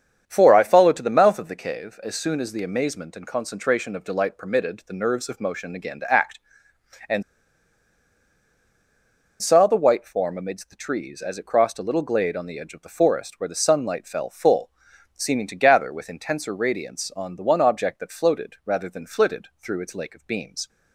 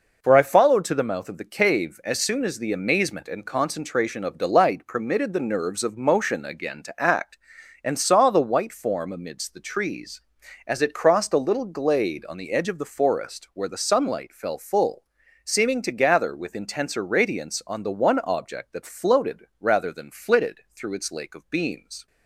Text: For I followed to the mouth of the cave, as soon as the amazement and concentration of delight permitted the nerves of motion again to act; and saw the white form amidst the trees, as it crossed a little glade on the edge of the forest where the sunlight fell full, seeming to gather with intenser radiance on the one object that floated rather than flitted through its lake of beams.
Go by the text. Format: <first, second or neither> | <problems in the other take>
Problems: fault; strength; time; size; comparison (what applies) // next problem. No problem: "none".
second | starts louder than the rest; strong; until 1.2 s; 8 dB // pauses between "and" and "saw"; strong; at 7.2 s; 2.1 s long